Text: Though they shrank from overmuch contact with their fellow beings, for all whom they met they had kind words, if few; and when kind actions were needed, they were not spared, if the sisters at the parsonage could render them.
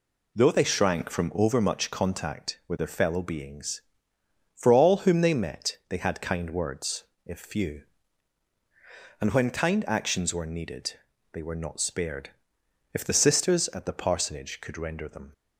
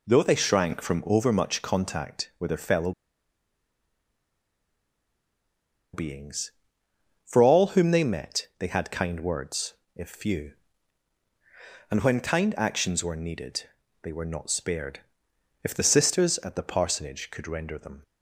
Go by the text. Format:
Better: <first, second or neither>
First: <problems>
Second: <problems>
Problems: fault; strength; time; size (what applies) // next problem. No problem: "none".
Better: first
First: none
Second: pauses between "fellow" and "beings"; strong; at 2.9 s; 3.0 s long